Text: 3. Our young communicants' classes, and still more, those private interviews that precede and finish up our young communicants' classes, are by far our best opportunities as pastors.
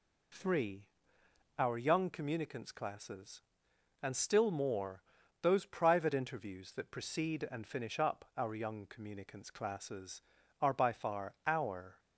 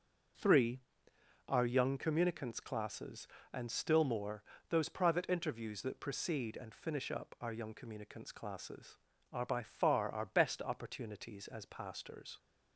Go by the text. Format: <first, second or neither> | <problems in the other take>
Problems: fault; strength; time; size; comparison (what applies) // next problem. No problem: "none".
second | stops before "best opportunities as pastors"; at 11.9 s